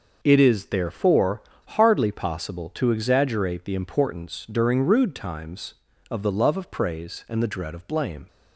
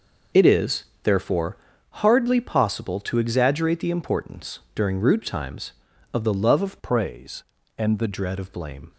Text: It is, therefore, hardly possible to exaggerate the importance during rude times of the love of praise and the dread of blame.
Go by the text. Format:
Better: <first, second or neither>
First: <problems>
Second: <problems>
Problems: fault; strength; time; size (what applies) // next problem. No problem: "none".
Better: first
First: none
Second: changes voice from "praise" to "the"; from 6.8 to 8.0 s; 1.2 s long